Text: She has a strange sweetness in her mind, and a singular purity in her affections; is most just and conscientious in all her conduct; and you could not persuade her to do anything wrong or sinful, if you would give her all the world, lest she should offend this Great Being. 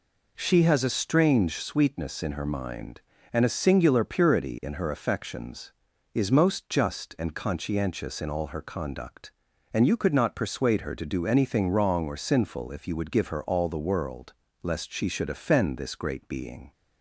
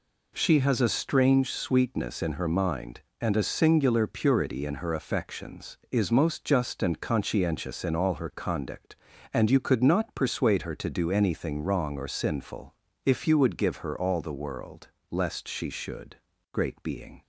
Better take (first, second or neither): first